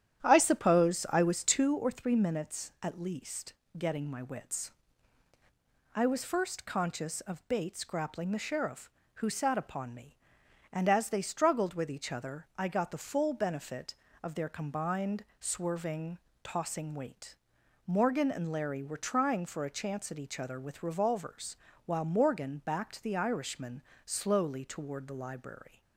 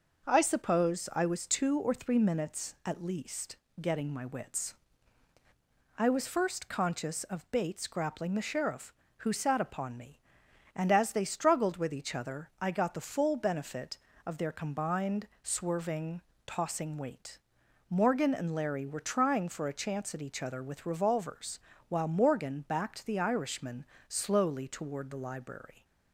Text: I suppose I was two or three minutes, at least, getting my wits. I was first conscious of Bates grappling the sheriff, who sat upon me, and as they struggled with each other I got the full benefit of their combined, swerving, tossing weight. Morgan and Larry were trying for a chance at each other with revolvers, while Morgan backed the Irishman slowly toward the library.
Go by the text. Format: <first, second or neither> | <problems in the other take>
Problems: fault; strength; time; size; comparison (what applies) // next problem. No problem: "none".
second | starts louder than the rest; strong; until 1.8 s; 10.5 dB // pauses between "Irishman" and "slowly"; slight; at 23.8 s; 0.24 s long; slight in the second